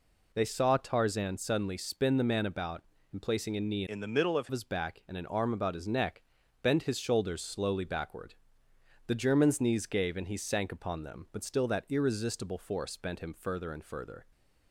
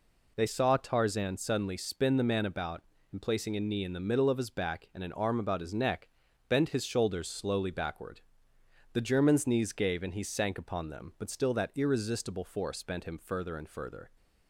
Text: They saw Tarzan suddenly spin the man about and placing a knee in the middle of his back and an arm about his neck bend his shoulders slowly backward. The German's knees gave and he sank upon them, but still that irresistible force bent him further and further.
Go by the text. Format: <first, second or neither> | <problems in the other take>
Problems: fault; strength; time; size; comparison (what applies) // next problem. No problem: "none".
second | changes voice from "in" to "of"; from 3.8 to 4.4 s; 0.6 s long // pauses between "neck" and "bend"; at 6.2 s; 0.40 s long; also in the second